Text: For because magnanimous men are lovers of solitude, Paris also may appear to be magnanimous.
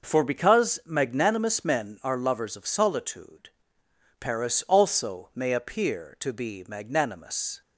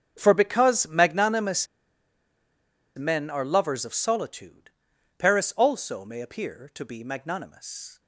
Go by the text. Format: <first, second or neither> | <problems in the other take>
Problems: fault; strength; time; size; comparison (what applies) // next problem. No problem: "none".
first | starts louder than the rest; strong; until 1.1 s; 7.5 dB // pauses between "magnanimous" and "men"; strong; at 1.6 s; 1.2 s long